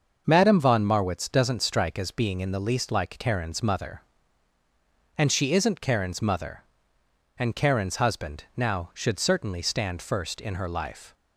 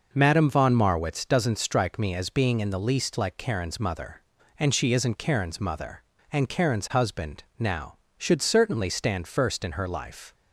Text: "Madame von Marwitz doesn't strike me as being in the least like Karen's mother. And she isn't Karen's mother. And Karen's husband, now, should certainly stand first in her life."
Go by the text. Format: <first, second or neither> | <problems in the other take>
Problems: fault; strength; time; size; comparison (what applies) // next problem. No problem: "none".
second | starts louder than the rest; until 1.2 s; 6 dB // skips "me"; at 1.9 s